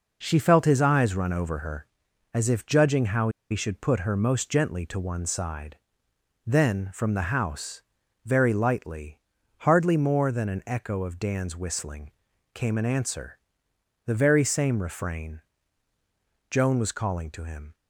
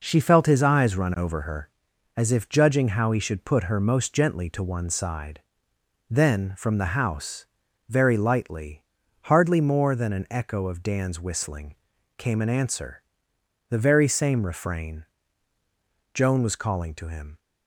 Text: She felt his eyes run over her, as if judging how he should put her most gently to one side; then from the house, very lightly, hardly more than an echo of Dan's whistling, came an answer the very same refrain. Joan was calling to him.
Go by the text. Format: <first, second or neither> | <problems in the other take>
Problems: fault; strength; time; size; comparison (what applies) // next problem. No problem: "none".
second | pauses between "how" and "he"; slight; at 3.2 s; 0.23 s long // pauses between "answer" and "the"; noticeable; at 13.3 s; 0.68 s long; noticeable in the second